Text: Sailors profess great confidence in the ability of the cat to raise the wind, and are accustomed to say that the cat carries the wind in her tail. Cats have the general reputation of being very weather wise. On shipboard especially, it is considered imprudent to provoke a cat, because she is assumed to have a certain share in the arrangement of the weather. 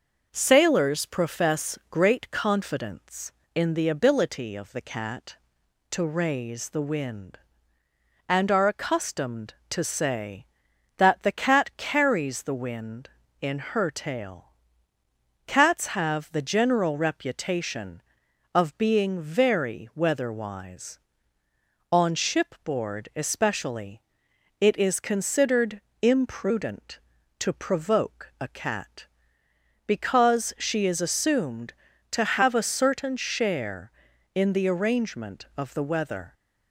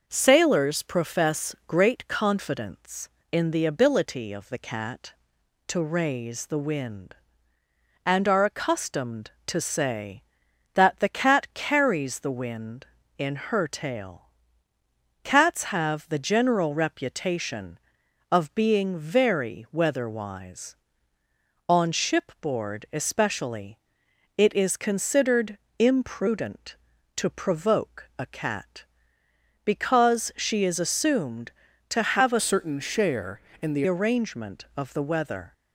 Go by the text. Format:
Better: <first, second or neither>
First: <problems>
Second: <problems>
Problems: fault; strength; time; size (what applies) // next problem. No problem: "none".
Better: first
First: pauses between "considered" and "imprudent"; slight; at 25.8 s; 0.22 s long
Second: pauses between "considered" and "imprudent"; slight; at 25.5 s; 0.22 s long // changes voice from "certain" to "the"; from 32.3 to 33.8 s; 1.5 s long